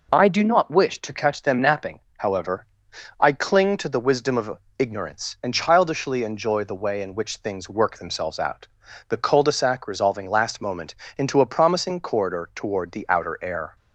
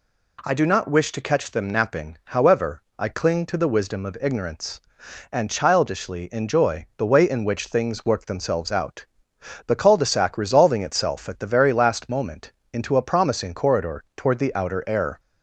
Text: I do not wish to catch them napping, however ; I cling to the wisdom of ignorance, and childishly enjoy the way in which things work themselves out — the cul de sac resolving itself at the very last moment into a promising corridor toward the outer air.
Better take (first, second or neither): second